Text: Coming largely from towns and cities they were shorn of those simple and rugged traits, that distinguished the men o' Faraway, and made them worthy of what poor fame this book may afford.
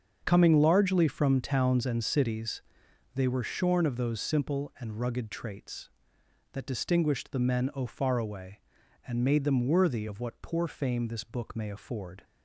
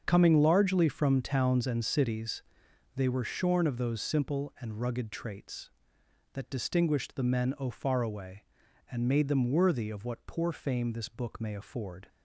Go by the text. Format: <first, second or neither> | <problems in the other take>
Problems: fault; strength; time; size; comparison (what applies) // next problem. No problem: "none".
neither | starts louder than the rest; the same in both // pauses between "cities" and "they"; noticeable; the same in both